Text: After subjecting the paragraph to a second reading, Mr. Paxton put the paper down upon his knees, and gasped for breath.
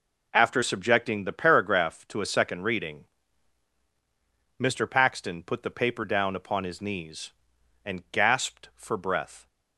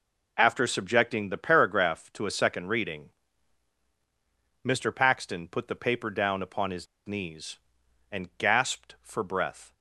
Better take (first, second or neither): first